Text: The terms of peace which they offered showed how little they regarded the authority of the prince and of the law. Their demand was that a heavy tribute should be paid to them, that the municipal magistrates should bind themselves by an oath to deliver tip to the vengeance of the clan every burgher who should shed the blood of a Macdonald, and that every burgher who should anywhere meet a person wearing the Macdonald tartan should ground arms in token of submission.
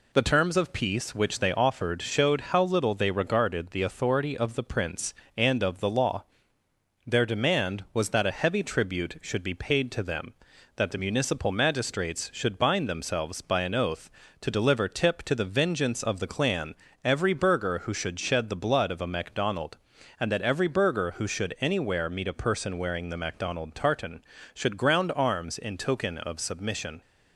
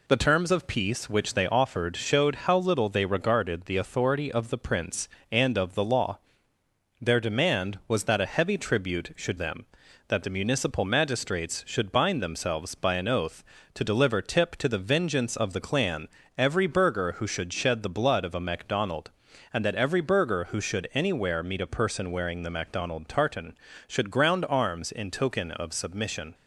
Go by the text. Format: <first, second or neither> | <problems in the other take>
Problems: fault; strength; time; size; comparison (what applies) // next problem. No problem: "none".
first | skips "be paid to"; at 9.3 s // pauses between "clan" and "every"; slight; at 16.0 s; 0.30 s long; slight in the first